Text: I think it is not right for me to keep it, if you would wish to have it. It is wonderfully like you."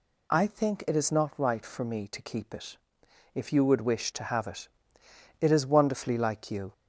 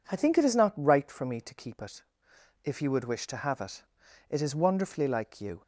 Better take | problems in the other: neither | none

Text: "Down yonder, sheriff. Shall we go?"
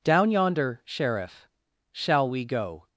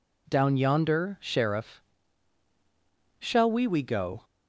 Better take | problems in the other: first | says "we" twice; at 3.6 s

